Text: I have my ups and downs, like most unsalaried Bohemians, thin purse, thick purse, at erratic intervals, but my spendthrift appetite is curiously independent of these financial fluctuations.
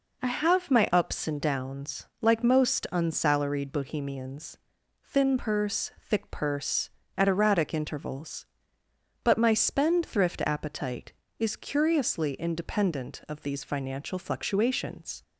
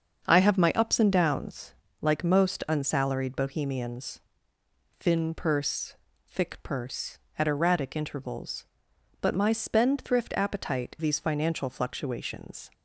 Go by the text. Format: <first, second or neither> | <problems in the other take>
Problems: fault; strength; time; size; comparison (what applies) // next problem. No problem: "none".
first | starts louder than the rest; until 1.3 s; 7 dB // skips "is curiously independent of"; at 10.9 s